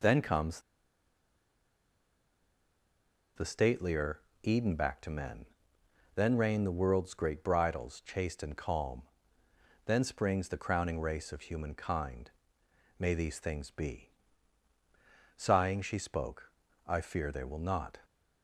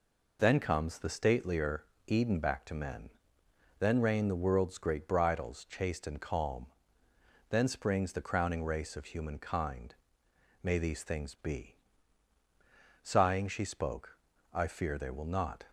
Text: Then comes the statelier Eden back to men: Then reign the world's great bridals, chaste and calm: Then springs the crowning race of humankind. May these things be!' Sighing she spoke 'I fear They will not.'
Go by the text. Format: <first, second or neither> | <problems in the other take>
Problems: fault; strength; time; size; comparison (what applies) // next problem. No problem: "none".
second | pauses between "comes" and "the"; strong; at 0.6 s; 2.7 s long // pauses between "statelier" and "Eden"; slight; at 4.2 s; 0.22 s long; slight in the second // pauses between "spoke" and "I"; slight; at 16.5 s; 0.36 s long; slight in the second